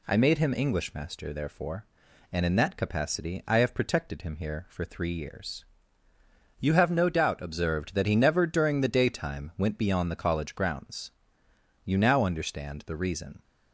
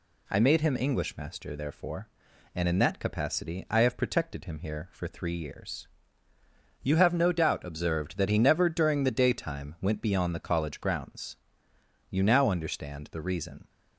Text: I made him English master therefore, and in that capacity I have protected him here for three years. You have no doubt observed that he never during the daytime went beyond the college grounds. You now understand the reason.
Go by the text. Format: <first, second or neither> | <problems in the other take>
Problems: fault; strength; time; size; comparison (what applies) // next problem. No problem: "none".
neither | none